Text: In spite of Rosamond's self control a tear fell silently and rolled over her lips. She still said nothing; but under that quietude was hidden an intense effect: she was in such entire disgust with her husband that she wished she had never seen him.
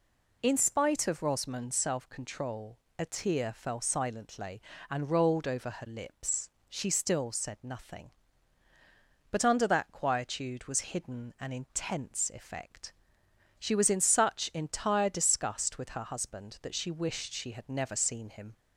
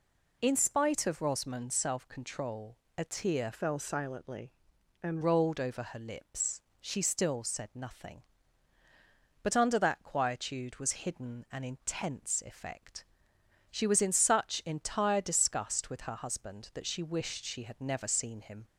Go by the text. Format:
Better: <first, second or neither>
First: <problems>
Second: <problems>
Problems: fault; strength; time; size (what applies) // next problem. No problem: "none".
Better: first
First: pauses between "control" and "a"; slight; at 2.7 s; 0.20 s long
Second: pauses between "control" and "a"; slight; at 2.7 s; 0.20 s long // changes voice from "fell" to "and"; from 3.5 to 5.2 s; 1.7 s long